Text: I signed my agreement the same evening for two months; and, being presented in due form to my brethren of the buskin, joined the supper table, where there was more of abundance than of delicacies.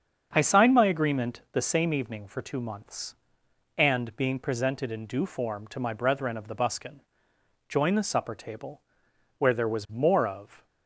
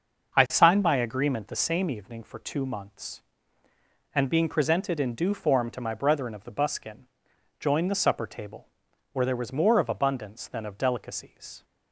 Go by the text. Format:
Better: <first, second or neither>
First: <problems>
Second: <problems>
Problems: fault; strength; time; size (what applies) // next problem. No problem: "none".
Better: second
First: starts louder than the rest; until 1.3 s; 7 dB // stops before "abundance than of delicacies"; at 10.6 s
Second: starts louder than the rest; until 1.4 s; 6 dB